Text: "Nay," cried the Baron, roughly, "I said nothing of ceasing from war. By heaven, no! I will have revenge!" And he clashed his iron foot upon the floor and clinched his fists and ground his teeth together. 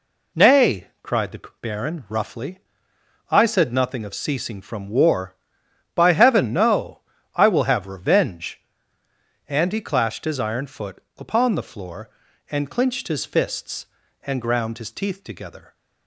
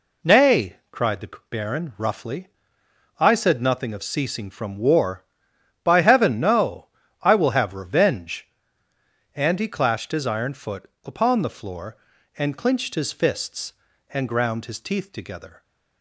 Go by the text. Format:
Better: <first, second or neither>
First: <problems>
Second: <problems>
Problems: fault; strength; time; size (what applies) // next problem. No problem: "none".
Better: neither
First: pauses between "the" and "Baron"; slight; at 1.4 s; 0.22 s long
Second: pauses between "the" and "Baron"; slight; at 1.2 s; 0.22 s long